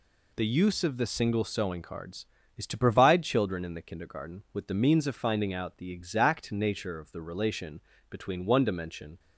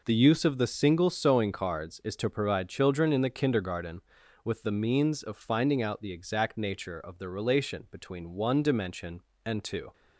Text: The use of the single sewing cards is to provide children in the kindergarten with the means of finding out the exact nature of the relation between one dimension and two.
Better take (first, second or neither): second